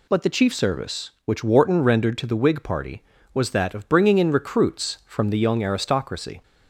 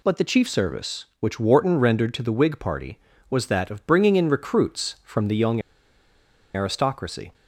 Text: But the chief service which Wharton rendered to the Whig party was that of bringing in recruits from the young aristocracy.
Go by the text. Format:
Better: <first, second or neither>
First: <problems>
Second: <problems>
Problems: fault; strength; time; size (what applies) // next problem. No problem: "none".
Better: first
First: none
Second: pauses between "young" and "aristocracy"; noticeable; at 5.6 s; 0.94 s long